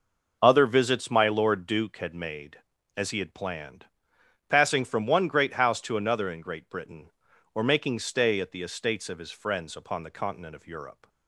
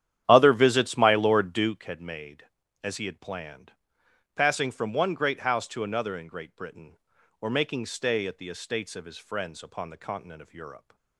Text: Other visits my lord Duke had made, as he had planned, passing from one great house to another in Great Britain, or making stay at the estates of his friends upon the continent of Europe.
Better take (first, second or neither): first